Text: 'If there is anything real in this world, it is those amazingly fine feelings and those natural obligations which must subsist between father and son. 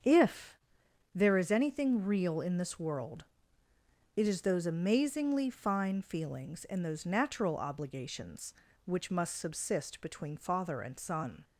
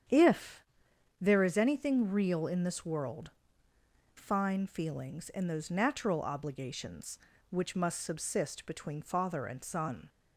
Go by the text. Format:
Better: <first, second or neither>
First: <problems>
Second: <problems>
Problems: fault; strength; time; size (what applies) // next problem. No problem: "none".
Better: first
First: starts louder than the rest; strong; until 1.6 s; 7 dB // pauses between "If" and "there"; noticeable; at 0.5 s; 0.56 s long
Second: starts louder than the rest; strong; until 1.6 s; 8.5 dB // pauses between "If" and "there"; noticeable; at 0.6 s; 0.56 s long // skips "it is those amazingly"; at 3.7 s